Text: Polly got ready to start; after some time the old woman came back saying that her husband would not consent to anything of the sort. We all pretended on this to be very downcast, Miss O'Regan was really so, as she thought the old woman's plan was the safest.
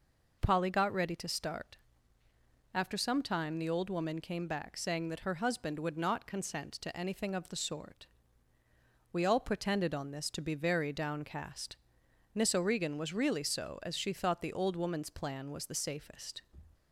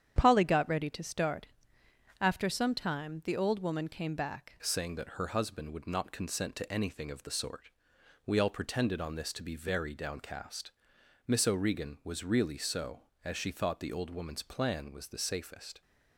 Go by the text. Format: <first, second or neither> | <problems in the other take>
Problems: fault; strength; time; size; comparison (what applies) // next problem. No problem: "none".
first | starts louder than the rest; strong; until 1.1 s; 9 dB // changes voice at "saying"; from 4.6 s on; 11.2 s long